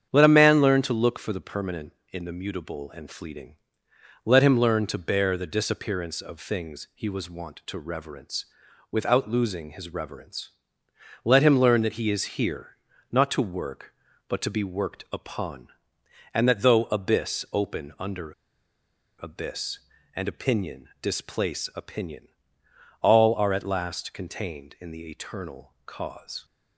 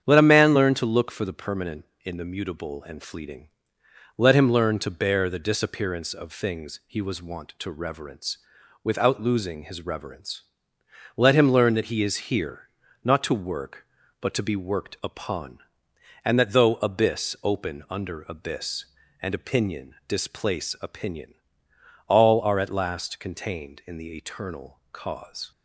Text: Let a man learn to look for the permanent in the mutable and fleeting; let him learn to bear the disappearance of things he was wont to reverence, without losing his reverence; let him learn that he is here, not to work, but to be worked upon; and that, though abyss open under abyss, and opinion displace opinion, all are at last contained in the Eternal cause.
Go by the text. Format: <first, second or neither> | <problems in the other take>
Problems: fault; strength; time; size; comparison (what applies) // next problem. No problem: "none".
second | starts louder than the rest; strong; until 1.1 s; 8.5 dB; strong in the second // pauses between "under" and "abyss"; noticeable; at 18.3 s; 0.92 s long